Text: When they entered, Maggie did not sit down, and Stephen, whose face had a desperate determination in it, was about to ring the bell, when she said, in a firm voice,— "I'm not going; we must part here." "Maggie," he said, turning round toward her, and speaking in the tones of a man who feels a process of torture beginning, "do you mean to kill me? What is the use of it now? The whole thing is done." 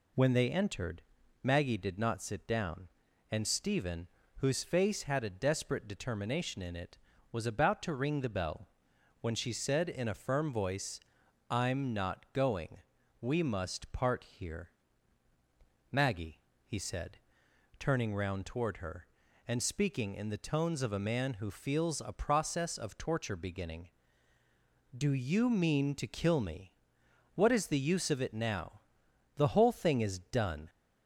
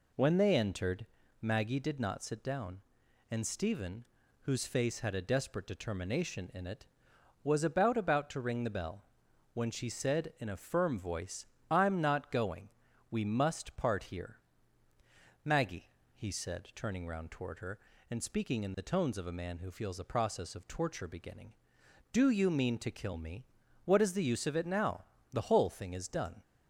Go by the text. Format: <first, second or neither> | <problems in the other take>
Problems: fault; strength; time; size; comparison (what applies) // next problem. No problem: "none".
first | says "about" twice; at 7.9 s